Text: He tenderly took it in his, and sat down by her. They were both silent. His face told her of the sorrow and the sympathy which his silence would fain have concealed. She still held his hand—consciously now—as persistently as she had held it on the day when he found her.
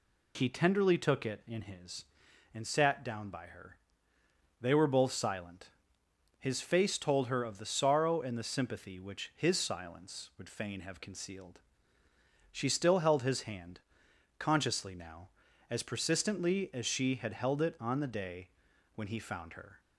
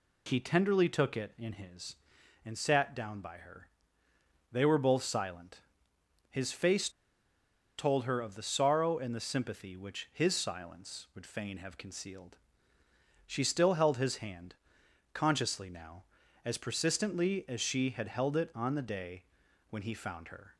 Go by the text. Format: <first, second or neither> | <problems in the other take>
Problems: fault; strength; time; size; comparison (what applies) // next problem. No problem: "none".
first | pauses between "face" and "told"; noticeable; at 6.8 s; 0.88 s long // pauses between "day" and "when"; at 19.2 s; 0.44 s long; also in the first